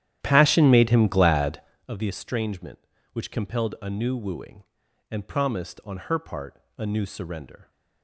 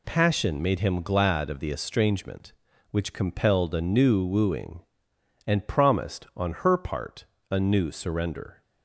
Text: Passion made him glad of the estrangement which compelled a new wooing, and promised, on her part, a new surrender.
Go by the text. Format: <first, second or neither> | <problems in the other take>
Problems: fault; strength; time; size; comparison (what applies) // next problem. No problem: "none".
second | starts louder than the rest; strong; until 1.8 s; 11.5 dB